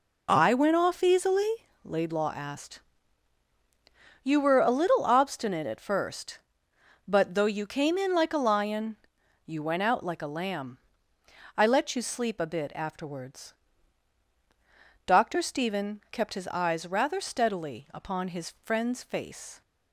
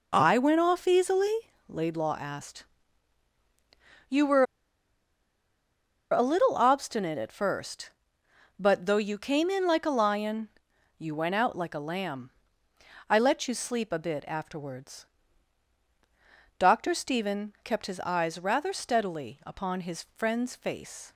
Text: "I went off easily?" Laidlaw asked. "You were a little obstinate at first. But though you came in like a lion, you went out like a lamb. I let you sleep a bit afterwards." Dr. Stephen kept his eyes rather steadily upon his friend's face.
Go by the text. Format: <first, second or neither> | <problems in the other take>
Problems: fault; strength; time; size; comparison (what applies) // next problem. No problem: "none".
first | pauses between "were" and "a"; strong; at 4.4 s; 1.6 s long